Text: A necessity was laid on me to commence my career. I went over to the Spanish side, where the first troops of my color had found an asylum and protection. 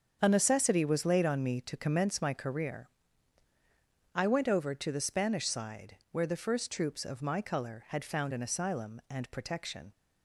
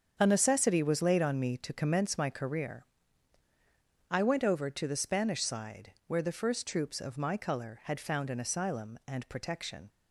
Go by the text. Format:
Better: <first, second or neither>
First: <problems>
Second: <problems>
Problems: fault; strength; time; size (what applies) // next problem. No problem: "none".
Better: neither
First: starts louder than the rest; until 1.2 s; 7 dB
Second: starts louder than the rest; until 1.1 s; 7 dB